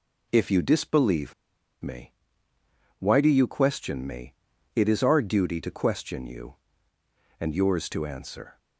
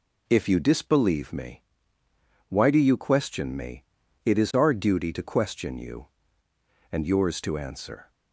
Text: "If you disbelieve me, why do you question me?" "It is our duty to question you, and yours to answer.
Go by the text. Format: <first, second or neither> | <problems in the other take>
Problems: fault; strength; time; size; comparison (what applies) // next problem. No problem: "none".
second | pauses between "disbelieve" and "me"; noticeable; at 1.3 s; 0.48 s long